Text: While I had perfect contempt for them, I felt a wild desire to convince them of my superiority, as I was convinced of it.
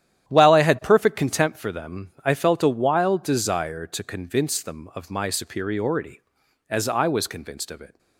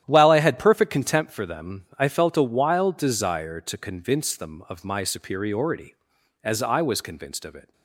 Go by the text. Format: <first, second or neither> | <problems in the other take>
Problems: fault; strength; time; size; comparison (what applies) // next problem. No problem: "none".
neither | starts louder than the rest; strong; the same in both